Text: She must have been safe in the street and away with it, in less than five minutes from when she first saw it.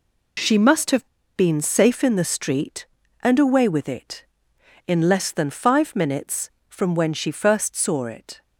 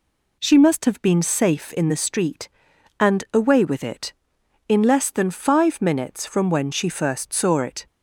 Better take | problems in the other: second | pauses between "have" and "been"; slight; at 1.0 s; 0.29 s long

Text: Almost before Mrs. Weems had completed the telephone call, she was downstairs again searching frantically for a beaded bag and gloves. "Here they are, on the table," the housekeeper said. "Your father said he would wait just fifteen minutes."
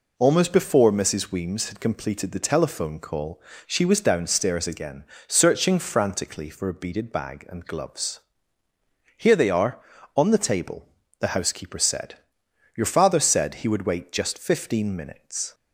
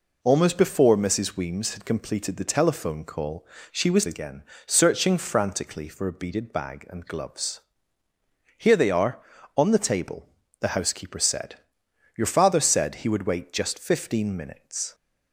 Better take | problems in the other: first | skips "downstairs"; at 4.0 s // pauses between "again" and "searching"; slight; at 4.4 s; 0.24 s long; slight in the first

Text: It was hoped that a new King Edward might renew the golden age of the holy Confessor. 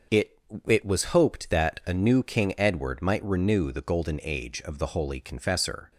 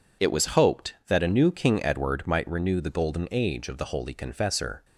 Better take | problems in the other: second | starts louder than the rest; until 1.3 s; 6 dB // says "It" twice; at 0.6 s

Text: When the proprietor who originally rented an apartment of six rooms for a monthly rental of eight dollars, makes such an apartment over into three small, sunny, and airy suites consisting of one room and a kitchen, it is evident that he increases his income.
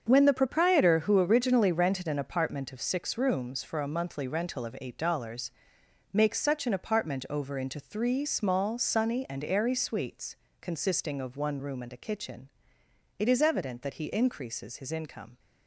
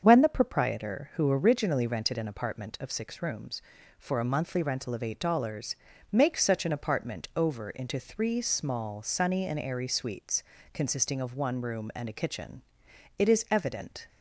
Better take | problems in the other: first | starts louder than the rest; until 1.0 s; 7 dB; also in the first // pauses between "suites" and "consisting"; slight; at 10.4 s; 0.32 s long; slight in the first // stops before "that he increases his income"; at 14.0 s

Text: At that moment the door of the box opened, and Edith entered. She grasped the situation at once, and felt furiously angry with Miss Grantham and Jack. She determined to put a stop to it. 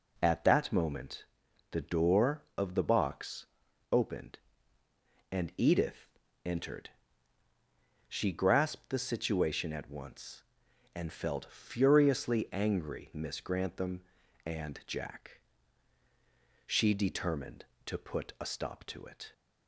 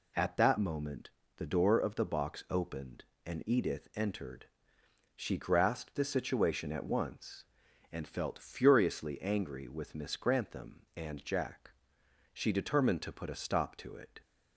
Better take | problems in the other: second | pauses between "moment" and "the"; noticeable; at 1.2 s; 0.46 s long; slight in the second // pauses between "box" and "opened"; noticeable; at 3.4 s; 0.46 s long // pauses between "Edith" and "entered"; slight; at 6.0 s; 0.36 s long // skips "with"; at 13.1 s

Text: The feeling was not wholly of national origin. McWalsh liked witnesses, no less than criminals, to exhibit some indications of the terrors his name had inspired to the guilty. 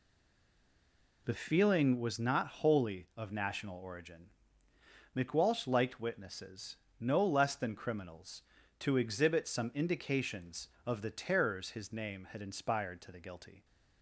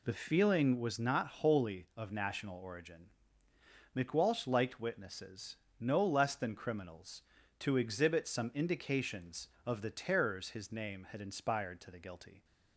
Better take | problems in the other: second | stays silent before the first word; noticeable; until 1.2 s; 1.2 s long

